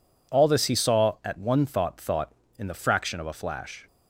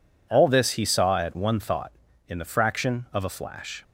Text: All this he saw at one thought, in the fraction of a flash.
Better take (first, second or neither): second